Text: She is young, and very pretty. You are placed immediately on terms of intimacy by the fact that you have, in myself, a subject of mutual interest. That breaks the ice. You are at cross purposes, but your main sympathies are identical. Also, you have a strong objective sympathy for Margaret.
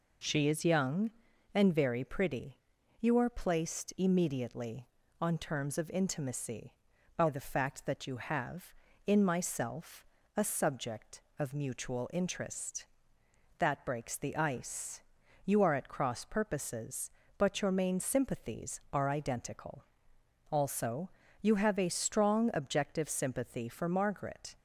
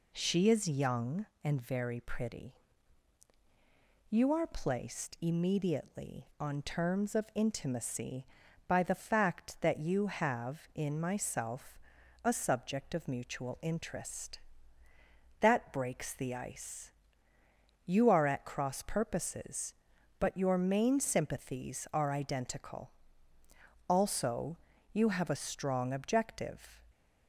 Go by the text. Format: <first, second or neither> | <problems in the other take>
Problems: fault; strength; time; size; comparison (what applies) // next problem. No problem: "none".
first | stops before "sympathy for Margaret"; at 26.9 s